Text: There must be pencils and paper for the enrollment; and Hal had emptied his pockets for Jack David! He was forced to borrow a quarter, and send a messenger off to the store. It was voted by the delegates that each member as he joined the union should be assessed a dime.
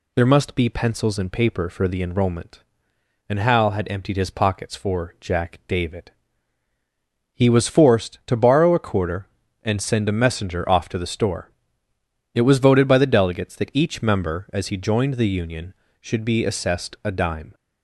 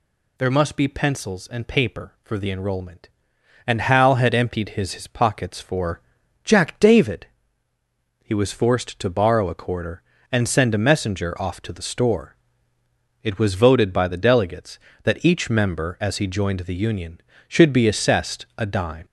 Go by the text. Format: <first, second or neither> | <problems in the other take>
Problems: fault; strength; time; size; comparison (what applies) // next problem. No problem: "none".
first | says "his" twice; at 4.9 s // pauses between "for" and "Jack"; at 6.0 s; 0.42 s long